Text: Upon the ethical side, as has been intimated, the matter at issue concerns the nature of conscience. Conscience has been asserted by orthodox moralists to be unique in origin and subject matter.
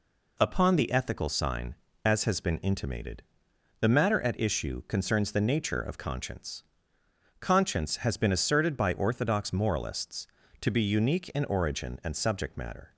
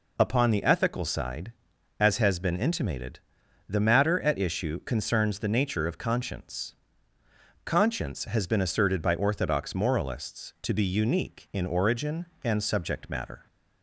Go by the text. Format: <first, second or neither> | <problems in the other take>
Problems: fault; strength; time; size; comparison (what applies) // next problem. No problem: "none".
second | says "sign" for "side"; at 1.2 s